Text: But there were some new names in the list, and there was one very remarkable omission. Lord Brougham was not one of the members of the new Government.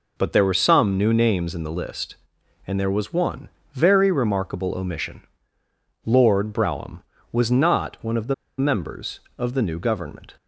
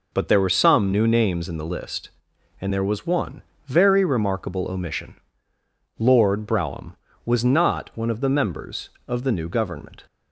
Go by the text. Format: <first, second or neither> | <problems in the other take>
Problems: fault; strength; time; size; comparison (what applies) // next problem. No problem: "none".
second | pauses between "one" and "very"; slight; at 3.4 s; 0.24 s long; slight in the second // pauses between "the" and "members"; slight; at 8.3 s; 0.24 s long